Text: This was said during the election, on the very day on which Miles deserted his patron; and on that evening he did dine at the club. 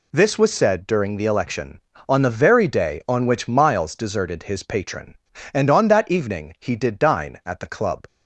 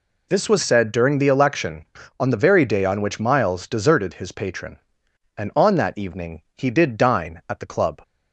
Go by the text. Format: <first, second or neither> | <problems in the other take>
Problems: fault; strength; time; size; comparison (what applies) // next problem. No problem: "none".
neither | none